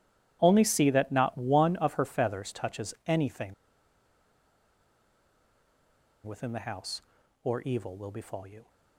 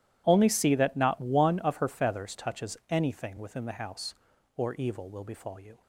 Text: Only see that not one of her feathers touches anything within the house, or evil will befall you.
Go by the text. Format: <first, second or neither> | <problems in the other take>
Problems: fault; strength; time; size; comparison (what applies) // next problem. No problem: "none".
second | pauses between "anything" and "within"; strong; at 3.5 s; 2.7 s long